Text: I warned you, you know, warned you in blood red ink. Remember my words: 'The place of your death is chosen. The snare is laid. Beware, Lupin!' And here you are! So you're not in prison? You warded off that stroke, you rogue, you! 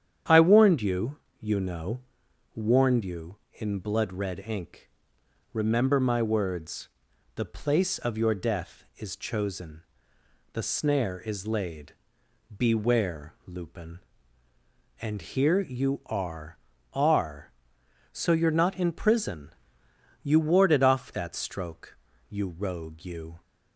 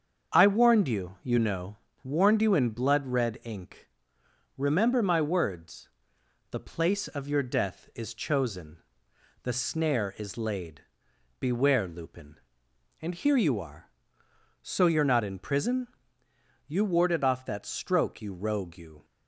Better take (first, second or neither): second